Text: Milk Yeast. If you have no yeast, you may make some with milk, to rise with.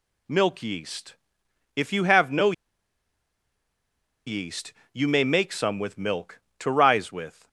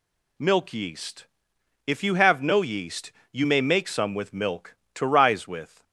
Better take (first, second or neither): second